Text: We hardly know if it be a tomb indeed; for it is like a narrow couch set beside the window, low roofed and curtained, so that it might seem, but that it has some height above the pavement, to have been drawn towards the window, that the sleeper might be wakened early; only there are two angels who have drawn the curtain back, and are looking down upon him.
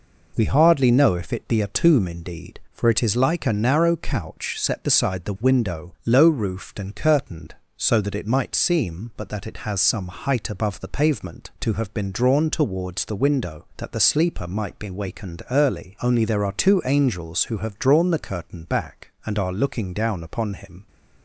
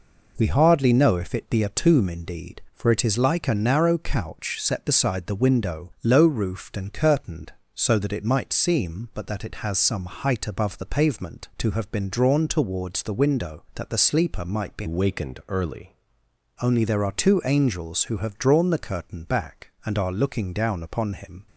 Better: first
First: none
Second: changes voice from "wakened" to "early"; from 14.8 to 15.9 s; 1.1 s long

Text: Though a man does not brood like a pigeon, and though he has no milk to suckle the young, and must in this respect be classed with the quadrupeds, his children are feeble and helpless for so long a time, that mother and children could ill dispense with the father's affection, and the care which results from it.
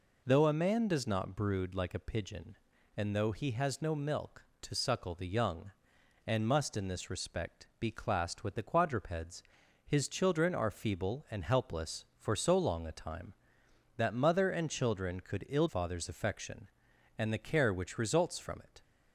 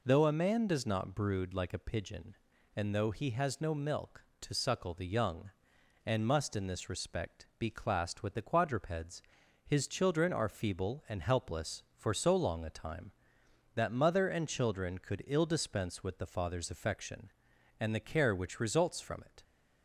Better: second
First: skips "dispense with the"; at 15.6 s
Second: none

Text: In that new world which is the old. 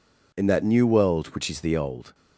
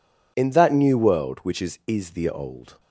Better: first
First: none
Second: says "is" twice; at 1.8 s

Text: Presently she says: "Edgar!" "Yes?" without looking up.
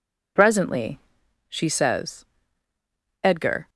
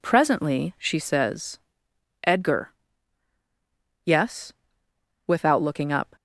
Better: second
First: pauses between "Presently" and "she"; noticeable; at 0.9 s; 0.50 s long // stops before "Yes without looking up"; at 3.6 s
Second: none

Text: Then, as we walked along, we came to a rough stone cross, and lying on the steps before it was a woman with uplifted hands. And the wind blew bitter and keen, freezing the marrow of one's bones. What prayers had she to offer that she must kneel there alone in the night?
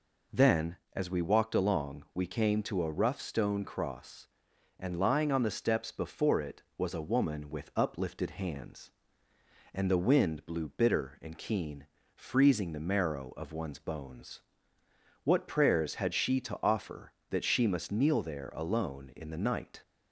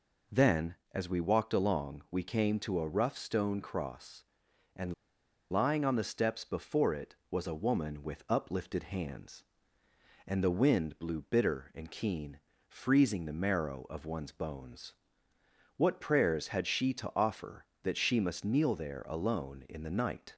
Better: first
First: none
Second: pauses between "and" and "lying"; noticeable; at 4.9 s; 0.58 s long

